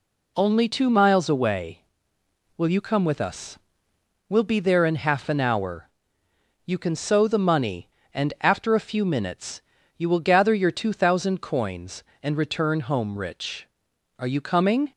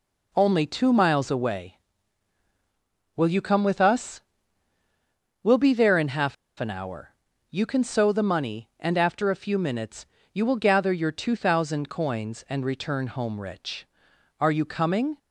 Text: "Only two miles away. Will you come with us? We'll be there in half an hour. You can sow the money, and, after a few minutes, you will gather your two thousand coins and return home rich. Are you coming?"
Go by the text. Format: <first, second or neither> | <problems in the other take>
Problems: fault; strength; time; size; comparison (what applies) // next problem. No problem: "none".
first | pauses between "half" and "an"; slight; at 6.3 s; 0.24 s long